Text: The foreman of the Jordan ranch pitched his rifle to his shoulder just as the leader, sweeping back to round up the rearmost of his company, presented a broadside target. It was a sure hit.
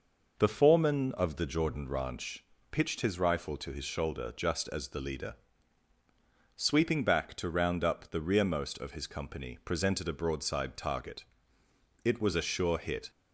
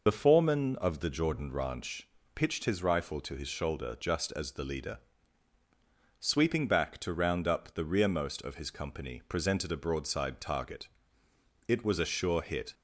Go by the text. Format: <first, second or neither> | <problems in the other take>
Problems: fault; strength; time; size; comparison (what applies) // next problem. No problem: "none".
first | loses the start of "The"; at 0.0 s; 45 ms // pauses between "ranch" and "pitched"; slight; at 2.0 s; 0.26 s long; slight in the first